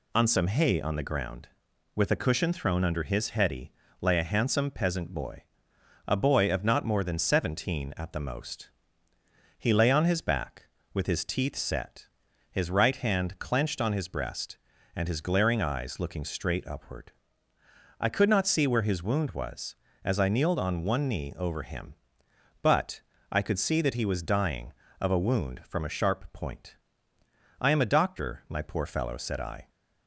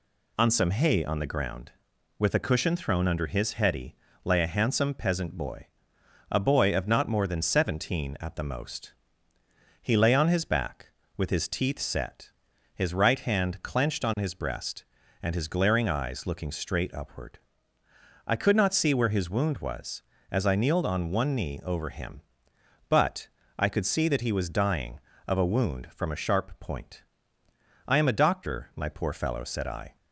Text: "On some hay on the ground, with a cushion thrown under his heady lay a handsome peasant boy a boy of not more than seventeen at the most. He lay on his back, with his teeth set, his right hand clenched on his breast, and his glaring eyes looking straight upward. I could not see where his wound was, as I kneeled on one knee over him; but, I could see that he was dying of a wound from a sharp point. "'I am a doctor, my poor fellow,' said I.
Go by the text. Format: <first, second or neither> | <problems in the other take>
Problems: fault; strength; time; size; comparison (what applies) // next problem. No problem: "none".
neither | pauses between "heady" and "lay"; slight; the same in both // pauses between "boy" and "a"; noticeable; the same in both